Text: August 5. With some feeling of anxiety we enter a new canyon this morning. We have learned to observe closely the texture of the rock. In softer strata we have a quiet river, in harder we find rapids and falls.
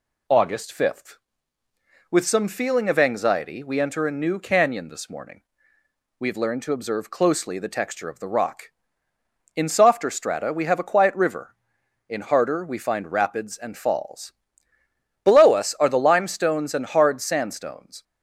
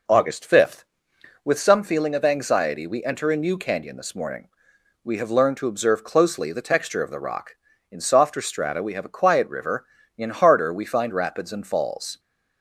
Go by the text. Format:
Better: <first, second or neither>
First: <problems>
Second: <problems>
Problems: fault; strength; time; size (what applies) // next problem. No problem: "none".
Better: second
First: goes on to say "Below us are the limestones and hard sandstones"; strong; from 15.2 s on; 2.8 s long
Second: none